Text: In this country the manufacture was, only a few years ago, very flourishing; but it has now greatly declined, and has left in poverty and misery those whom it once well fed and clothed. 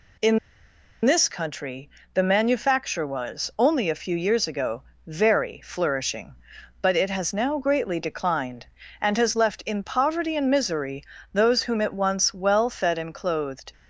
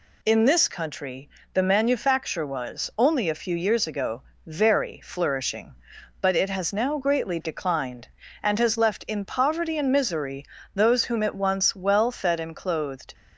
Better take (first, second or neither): second